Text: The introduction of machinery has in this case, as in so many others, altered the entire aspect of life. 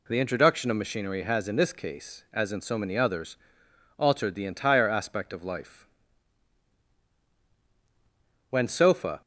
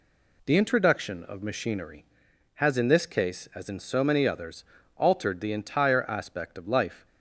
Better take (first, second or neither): second